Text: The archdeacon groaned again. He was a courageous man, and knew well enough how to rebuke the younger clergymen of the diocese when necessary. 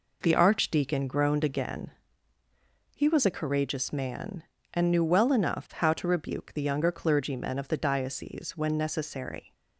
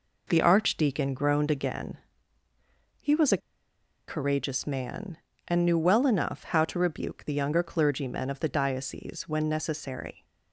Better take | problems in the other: first | pauses between "a" and "courageous"; noticeable; at 3.3 s; 0.69 s long

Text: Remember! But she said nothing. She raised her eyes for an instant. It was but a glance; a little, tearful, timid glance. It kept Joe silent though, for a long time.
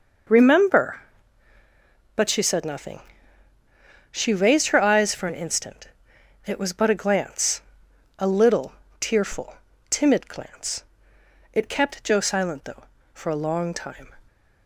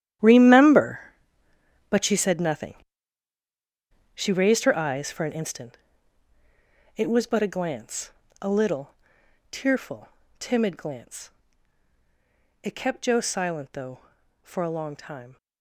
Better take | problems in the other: first | gets quieter; strong; throughout; 14.5 dB

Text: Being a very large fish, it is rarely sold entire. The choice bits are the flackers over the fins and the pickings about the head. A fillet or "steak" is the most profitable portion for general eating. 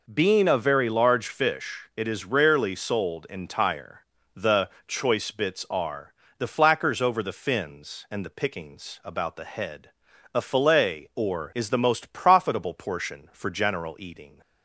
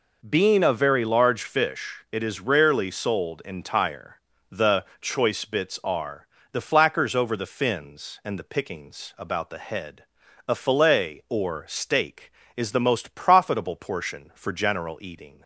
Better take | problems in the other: second | pauses between "The" and "choice"; slight; at 4.6 s; 0.16 s long; slight in the second // pauses between "are" and "the"; slight; at 6.1 s; 0.26 s long; slight in the second // skips "steak"; at 11.5 s

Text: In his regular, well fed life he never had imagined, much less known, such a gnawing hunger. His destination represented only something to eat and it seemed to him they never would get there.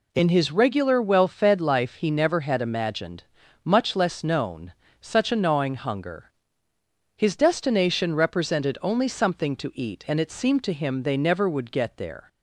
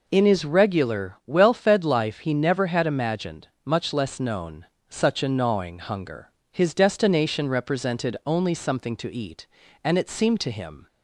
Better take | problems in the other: first | stops before "they never would get there"; at 10.8 s

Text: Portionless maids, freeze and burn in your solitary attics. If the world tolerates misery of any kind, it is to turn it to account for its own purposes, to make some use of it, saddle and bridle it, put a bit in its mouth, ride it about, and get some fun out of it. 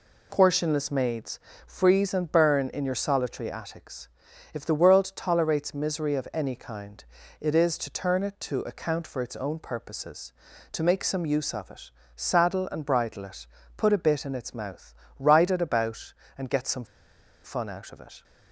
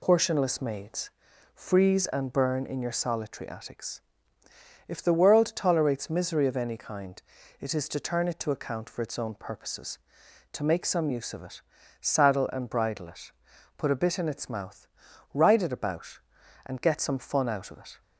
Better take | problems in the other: second | pauses between "some" and "fun"; noticeable; at 16.8 s; 0.59 s long

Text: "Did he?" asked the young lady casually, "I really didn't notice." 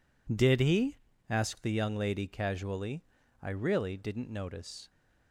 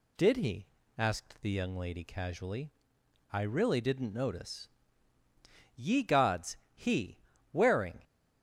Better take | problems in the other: first | goes on to say "Ye Gods He wearing"; strong; from 5.7 s on; 2.2 s long

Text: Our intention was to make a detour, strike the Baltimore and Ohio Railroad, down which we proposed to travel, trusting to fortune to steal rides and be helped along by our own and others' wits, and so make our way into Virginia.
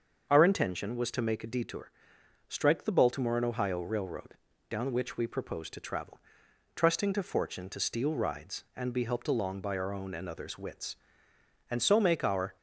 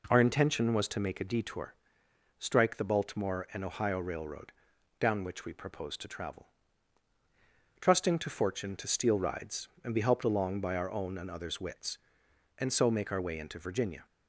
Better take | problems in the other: second | starts louder than the rest; until 1.3 s; 6.5 dB // stops before "way into Virginia"; at 12.5 s

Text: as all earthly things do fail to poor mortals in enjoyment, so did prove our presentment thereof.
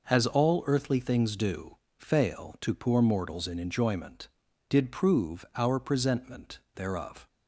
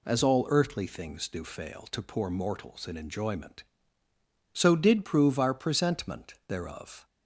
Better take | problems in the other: second | pauses between "do" and "fail"; slight; at 1.7 s; 0.22 s long // skips "so"; at 4.4 s // pauses between "presentment" and "thereof"; slight; at 6.5 s; 0.16 s long

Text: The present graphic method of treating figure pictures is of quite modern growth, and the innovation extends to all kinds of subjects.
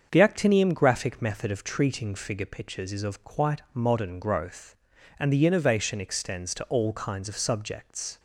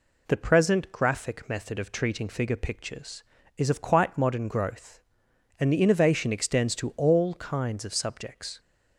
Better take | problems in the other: second | starts louder than the rest; until 1.1 s; 6.5 dB // says "actinium" for "present"; at 0.2 s

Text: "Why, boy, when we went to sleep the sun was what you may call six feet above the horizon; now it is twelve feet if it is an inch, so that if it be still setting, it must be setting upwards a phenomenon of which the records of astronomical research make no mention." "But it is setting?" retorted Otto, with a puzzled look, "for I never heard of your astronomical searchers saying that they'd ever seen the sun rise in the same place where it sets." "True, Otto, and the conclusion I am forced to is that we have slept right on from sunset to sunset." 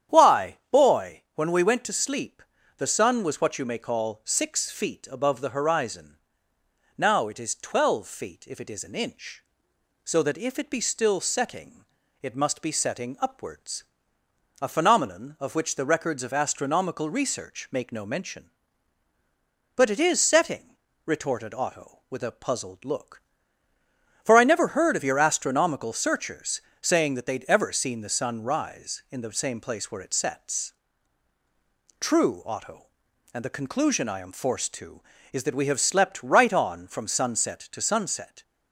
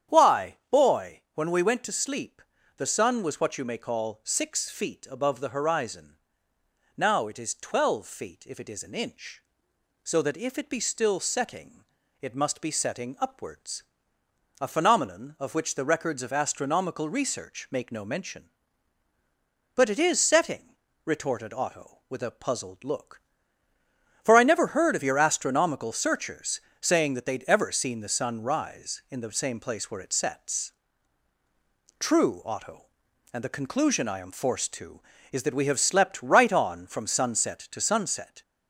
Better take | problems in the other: first | gets louder; slight; throughout; 2 dB // starts louder than the rest; strong; until 1.3 s; 9 dB; strong in the first // pauses between "sleep" and "the"; slight; at 2.4 s; 0.36 s long; slight in the first // pauses between "upwards" and "a"; noticeable; at 13.8 s; 0.78 s long; noticeable in the first // pauses between "searchers" and "saying"; slight; at 26.5 s; 0.22 s long; slight in the first

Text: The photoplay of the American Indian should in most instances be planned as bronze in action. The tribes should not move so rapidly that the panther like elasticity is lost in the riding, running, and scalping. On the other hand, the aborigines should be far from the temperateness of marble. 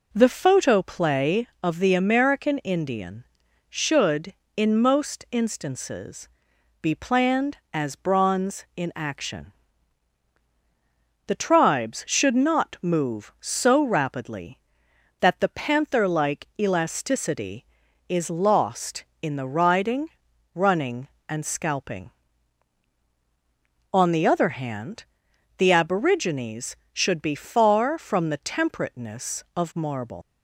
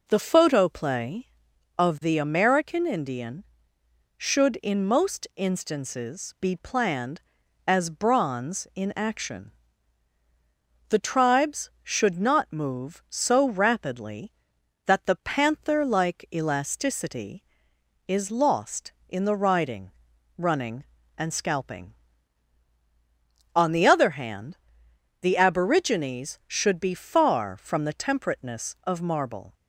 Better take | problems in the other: second | pauses between "instances" and "be"; noticeable; at 6.2 s; 0.54 s long // leaves "marble" unfinished; at 30.2 s; 120 ms

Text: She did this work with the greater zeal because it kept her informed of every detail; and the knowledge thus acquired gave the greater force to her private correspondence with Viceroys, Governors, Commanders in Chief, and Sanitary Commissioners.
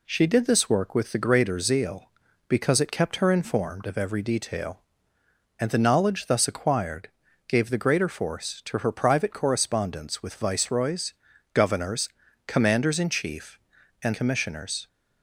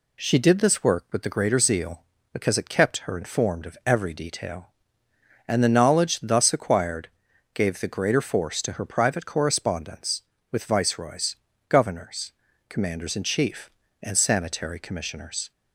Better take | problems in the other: second | pauses between "acquired" and "gave"; at 7.0 s; 0.40 s long; also in the second // skips "Sanitary"; at 14.1 s

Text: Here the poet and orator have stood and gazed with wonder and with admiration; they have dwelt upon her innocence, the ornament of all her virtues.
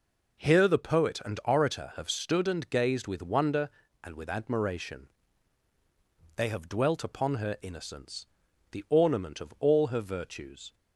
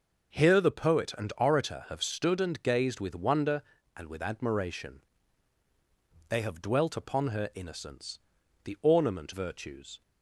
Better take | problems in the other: first | starts louder than the rest; until 1.4 s; 6.5 dB // skips "of all her"; at 9.3 s

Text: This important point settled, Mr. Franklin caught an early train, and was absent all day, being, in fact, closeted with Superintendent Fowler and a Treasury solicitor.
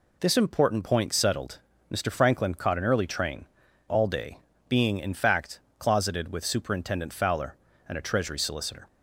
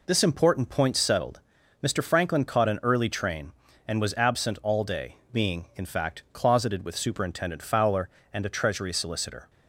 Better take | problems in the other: second | skips "and was absent"; at 3.6 s

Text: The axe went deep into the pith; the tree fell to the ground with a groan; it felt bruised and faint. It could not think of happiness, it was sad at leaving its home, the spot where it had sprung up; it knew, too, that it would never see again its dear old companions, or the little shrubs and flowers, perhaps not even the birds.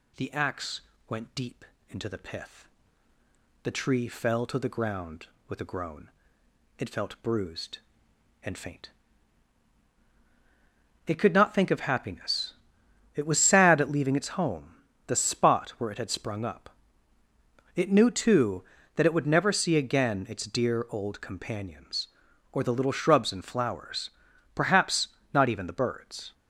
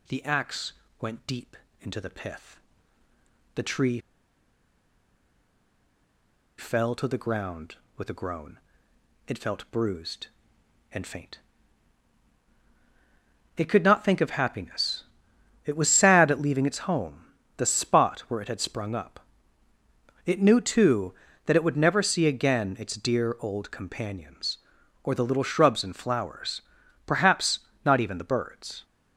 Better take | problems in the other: first | pauses between "axe" and "went"; slight; at 0.7 s; 0.28 s long; slight in the first // pauses between "deep" and "into"; slight; at 1.5 s; 0.26 s long; slight in the first // pauses between "tree" and "fell"; strong; at 3.9 s; 2.5 s long // pauses between "perhaps" and "not"; slight; at 27.5 s; 0.24 s long; slight in the first

